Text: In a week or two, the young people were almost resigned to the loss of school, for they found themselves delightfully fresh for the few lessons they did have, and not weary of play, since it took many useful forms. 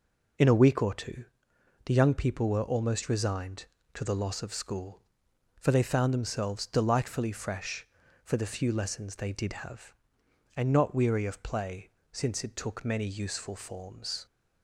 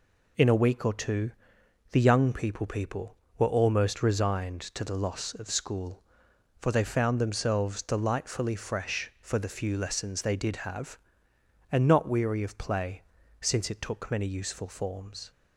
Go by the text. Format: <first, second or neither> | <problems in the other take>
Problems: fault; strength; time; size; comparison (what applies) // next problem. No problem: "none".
first | says "people" twice; at 2.6 s